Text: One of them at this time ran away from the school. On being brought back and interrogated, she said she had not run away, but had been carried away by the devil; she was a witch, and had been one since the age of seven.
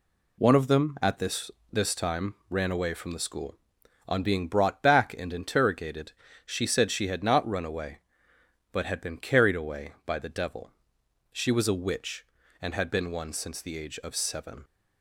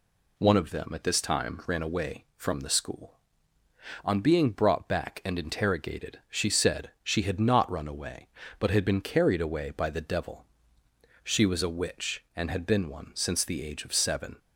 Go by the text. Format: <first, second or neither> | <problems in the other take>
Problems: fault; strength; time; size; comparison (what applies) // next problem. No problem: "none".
second | says "this" twice; at 1.7 s // pauses between "time" and "ran"; slight; at 2.3 s; 0.16 s long